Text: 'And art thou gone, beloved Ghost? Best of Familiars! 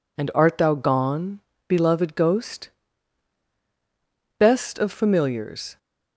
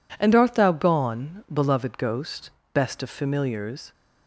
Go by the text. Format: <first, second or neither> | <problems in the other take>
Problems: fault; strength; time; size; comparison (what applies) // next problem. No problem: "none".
neither | none